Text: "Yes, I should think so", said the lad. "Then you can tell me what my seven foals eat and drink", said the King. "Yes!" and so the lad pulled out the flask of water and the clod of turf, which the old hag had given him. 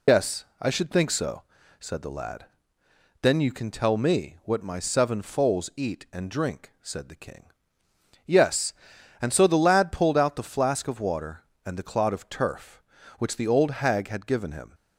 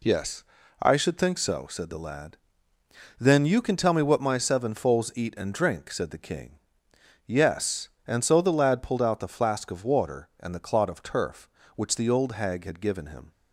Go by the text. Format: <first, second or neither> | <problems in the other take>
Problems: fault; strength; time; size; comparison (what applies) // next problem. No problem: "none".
second | loses the start of "Yes"; at 0.0 s; 115 ms